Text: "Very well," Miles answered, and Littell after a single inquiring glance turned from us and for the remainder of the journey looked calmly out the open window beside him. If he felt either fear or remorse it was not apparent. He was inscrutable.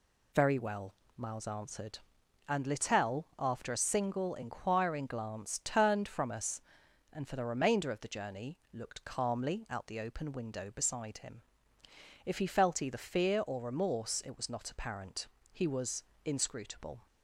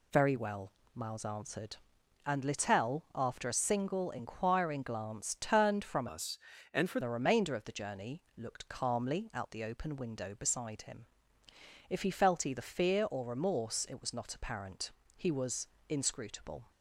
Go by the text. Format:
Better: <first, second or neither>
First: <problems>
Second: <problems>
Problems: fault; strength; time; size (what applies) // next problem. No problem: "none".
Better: first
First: pauses between "was" and "inscrutable"; slight; at 16.0 s; 0.22 s long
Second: changes voice from "us" to "for"; from 6.0 to 6.9 s; 0.9 s long // pauses between "was" and "inscrutable"; slight; at 15.6 s; 0.22 s long